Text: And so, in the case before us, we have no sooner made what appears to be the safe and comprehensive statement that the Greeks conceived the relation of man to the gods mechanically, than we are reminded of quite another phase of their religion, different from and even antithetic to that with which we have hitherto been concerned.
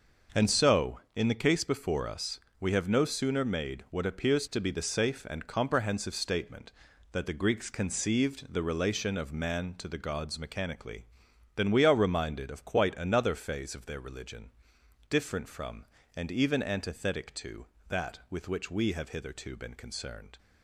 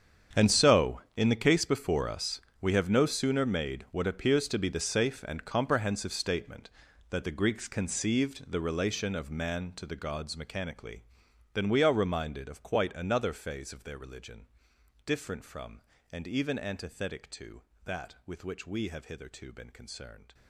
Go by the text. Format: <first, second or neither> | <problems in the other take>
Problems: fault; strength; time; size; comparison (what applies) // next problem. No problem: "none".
first | gets quieter; strong; throughout; 17 dB